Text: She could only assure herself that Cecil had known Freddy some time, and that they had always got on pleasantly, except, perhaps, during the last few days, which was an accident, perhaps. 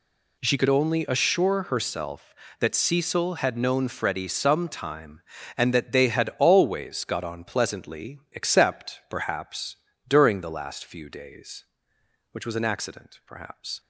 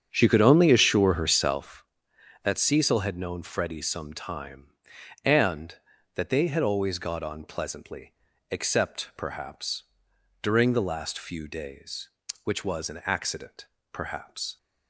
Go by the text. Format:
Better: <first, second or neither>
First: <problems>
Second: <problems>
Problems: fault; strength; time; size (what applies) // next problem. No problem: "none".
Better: first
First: none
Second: starts louder than the rest; strong; until 1.9 s; 8.5 dB